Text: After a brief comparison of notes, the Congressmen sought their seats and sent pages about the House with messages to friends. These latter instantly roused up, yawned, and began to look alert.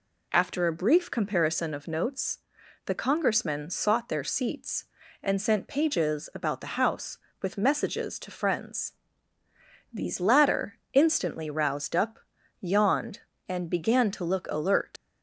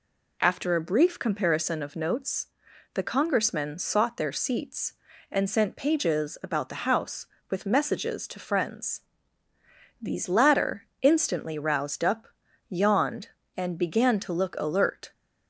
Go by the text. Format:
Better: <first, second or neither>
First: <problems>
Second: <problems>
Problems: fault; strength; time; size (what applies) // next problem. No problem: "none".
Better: second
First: pauses between "latter" and "instantly"; slight; at 10.7 s; 0.16 s long // leaves "alert" unfinished; at 14.9 s; 75 ms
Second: pauses between "latter" and "instantly"; slight; at 10.8 s; 0.16 s long